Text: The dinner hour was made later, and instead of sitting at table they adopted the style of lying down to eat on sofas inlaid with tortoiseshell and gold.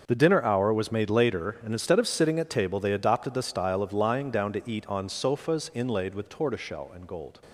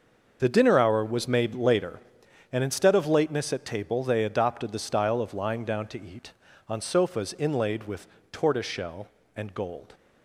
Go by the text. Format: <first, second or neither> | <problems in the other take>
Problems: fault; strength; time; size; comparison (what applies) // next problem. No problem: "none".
first | starts louder than the rest; until 1.4 s; 6.5 dB; also in the first // says "lateness" for "sitting"; at 3.0 s // pauses between "with" and "tortoiseshell"; slight; at 8.0 s; 0.26 s long